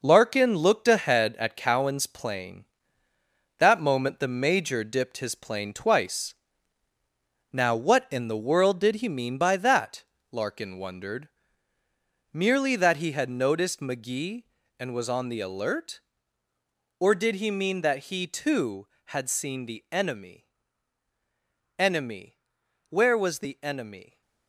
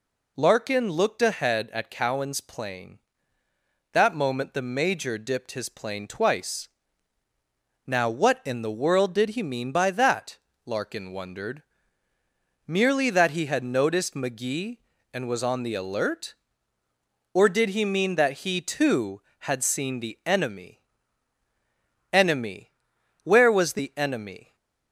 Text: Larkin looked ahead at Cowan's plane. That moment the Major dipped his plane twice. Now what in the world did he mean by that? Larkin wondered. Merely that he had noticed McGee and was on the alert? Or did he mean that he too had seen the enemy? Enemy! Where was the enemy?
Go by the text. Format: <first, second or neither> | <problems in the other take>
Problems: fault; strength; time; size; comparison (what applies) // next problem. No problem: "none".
second | gets quieter; strong; throughout; 8 dB